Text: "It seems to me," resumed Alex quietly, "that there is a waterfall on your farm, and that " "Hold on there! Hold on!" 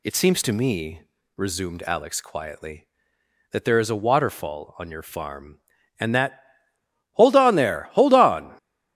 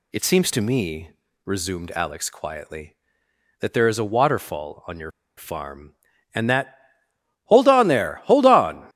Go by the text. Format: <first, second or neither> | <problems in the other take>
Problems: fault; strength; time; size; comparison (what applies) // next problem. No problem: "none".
first | pauses between "your" and "farm"; slight; at 5.1 s; 0.26 s long